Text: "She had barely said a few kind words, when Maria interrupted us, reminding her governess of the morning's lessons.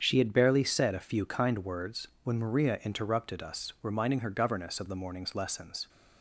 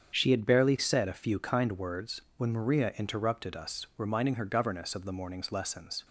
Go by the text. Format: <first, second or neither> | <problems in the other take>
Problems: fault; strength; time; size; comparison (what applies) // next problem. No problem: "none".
neither | starts louder than the rest; strong; the same in both